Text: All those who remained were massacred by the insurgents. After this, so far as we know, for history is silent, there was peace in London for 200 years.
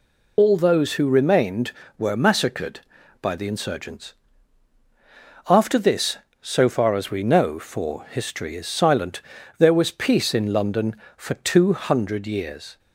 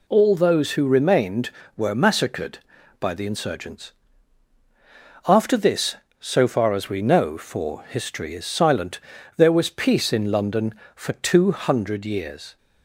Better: second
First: loses the start of "All"; at 0.3 s; 75 ms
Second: none

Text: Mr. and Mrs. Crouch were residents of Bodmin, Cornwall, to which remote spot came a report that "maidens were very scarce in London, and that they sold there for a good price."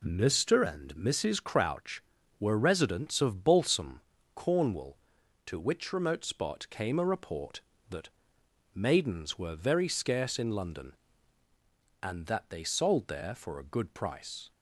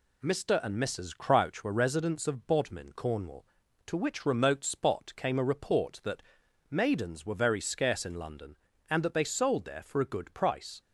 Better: second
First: says "Balsam" for "Bodmin"; at 3.4 s // pauses between "that" and "maidens"; noticeable; at 8.0 s; 0.66 s long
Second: pauses between "that" and "maidens"; noticeable; at 6.2 s; 0.48 s long

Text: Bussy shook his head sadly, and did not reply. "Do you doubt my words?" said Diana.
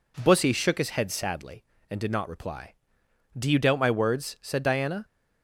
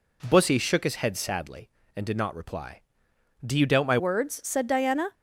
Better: first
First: none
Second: changes voice at "words"; from 3.9 s on; 1.2 s long

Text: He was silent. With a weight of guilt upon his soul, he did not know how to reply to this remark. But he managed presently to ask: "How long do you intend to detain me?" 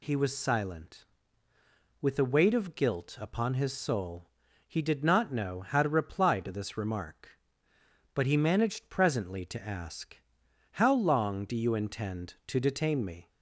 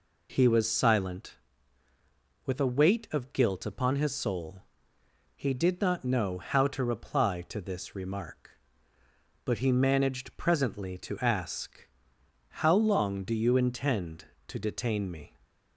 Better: neither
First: none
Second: none

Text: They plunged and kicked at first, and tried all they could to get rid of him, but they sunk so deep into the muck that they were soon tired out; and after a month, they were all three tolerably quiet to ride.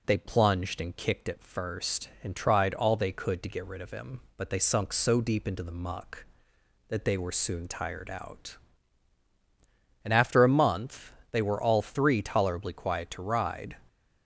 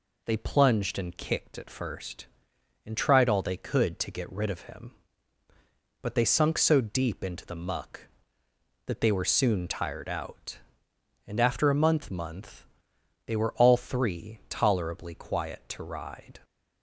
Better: first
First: none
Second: says "month" twice; at 12.0 s

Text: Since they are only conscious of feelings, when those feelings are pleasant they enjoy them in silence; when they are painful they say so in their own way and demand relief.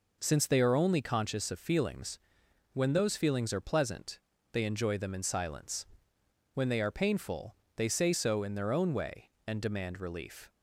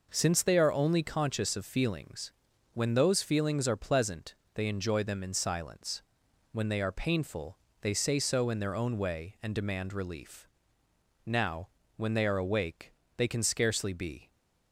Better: first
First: pauses between "pleasant" and "they"; slight; at 4.1 s; 0.32 s long // pauses between "painful" and "they"; slight; at 7.5 s; 0.22 s long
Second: pauses between "pleasant" and "they"; slight; at 4.3 s; 0.22 s long // pauses between "painful" and "they"; slight; at 7.5 s; 0.24 s long // goes on to say "Now when they are awake they can scarcely be"; strong; from 11.2 s on; 3.0 s long

